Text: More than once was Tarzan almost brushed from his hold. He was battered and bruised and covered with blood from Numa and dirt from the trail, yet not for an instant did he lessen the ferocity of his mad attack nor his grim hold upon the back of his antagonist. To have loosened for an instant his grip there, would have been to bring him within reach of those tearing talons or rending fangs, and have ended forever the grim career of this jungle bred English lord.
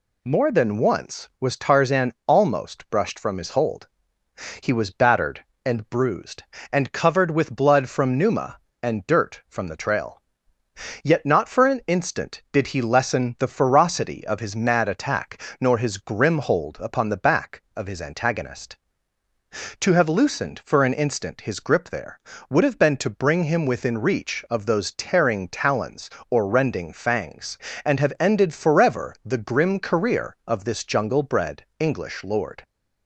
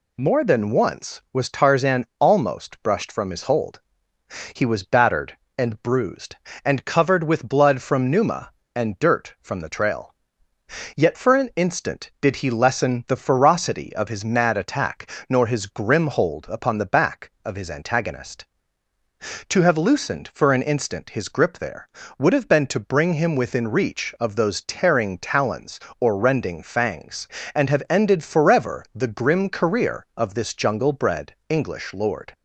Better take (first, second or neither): first